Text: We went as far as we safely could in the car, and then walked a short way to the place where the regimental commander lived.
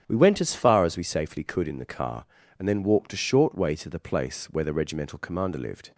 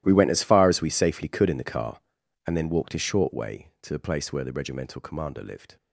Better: first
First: starts louder than the rest; strong; until 1.0 s; 9 dB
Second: gets quieter; strong; throughout; 17.5 dB // starts louder than the rest; strong; until 1.0 s; 14 dB

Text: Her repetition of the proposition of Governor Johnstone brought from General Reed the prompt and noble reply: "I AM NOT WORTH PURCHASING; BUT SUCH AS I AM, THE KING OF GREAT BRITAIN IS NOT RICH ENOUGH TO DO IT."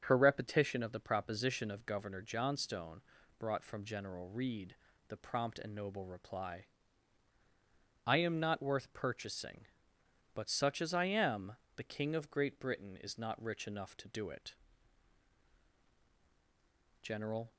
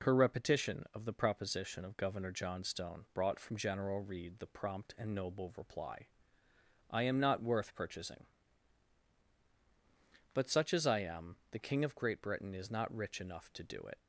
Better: second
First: starts louder than the rest; until 1.0 s; 7 dB // pauses between "Johnstone" and "brought"; at 2.9 s; 0.40 s long // pauses between "Reed" and "the"; slight; at 4.7 s; 0.32 s long // goes on to say "General"; from 17.0 s on; 0.52 s long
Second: none

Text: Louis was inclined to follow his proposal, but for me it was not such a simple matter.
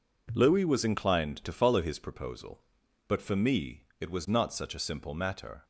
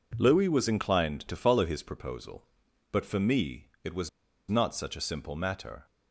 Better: first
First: none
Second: pauses between "was" and "not"; at 4.0 s; 0.40 s long

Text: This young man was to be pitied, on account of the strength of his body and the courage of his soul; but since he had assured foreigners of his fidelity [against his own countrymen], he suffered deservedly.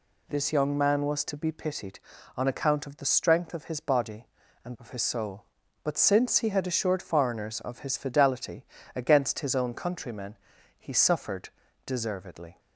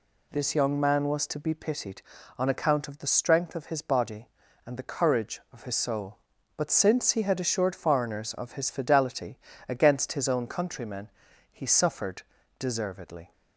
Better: second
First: skips "the courage"; at 4.7 s // pauses between "fidelity" and "against"; slight; at 8.6 s; 0.32 s long // pauses between "suffered" and "deservedly"; slight; at 11.5 s; 0.34 s long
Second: pauses between "fidelity" and "against"; slight; at 9.3 s; 0.32 s long // pauses between "suffered" and "deservedly"; slight; at 12.2 s; 0.34 s long

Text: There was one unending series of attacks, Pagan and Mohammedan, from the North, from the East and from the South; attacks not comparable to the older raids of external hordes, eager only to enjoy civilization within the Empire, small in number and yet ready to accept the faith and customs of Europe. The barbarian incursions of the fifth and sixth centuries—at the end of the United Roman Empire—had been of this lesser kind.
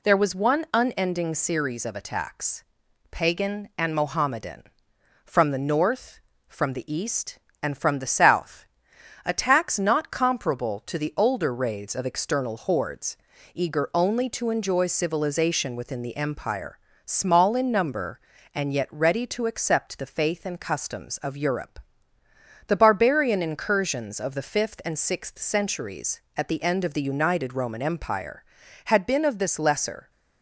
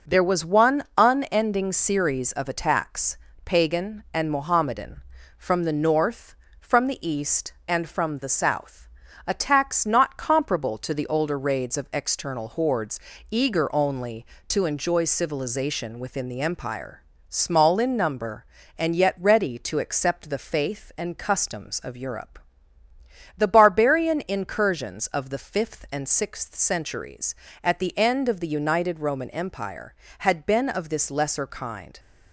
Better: second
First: stops before "kind"; at 30.0 s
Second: none

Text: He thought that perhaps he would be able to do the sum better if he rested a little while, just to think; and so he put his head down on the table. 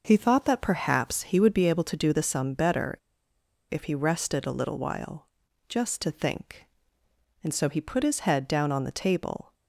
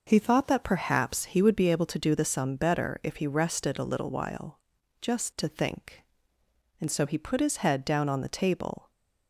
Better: second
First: pauses between "better" and "if"; noticeable; at 2.9 s; 0.75 s long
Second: none

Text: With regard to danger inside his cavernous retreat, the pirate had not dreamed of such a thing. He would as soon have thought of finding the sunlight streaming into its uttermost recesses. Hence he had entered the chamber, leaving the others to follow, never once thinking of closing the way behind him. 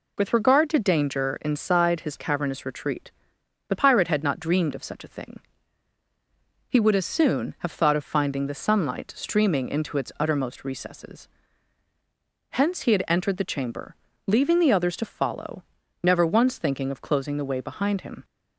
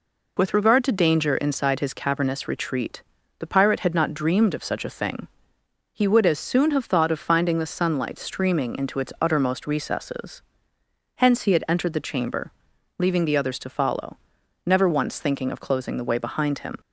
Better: neither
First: none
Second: none

